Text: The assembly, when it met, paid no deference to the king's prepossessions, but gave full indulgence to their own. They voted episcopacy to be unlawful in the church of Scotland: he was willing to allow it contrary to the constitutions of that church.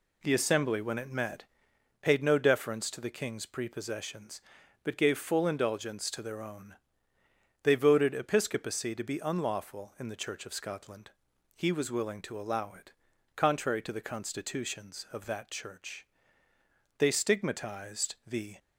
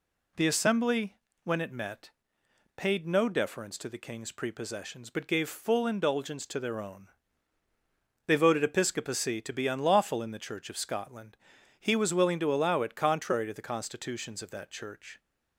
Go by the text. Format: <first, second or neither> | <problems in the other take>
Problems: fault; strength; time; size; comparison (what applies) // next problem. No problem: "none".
second | pauses between "it" and "contrary"; noticeable; at 12.9 s; 0.46 s long // goes on to say "They stigmatized the"; from 16.9 s on; 1.6 s long